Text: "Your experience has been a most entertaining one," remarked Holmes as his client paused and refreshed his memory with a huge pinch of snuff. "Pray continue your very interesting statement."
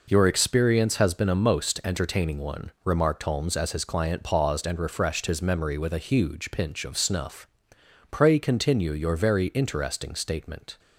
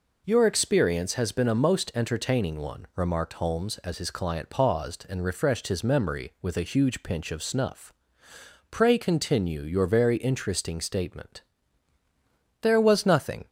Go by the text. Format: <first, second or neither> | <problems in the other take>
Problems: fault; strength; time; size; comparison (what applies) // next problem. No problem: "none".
first | goes on to say "There was nothing"; noticeable; from 12.6 s on; 0.86 s long